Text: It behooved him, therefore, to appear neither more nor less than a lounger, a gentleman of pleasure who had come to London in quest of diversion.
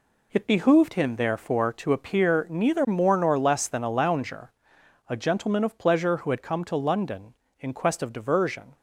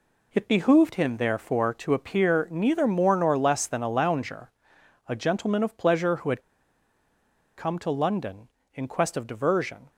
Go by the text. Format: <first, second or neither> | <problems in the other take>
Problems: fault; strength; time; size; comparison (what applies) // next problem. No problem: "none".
first | pauses between "had" and "come"; at 6.4 s; 1.1 s long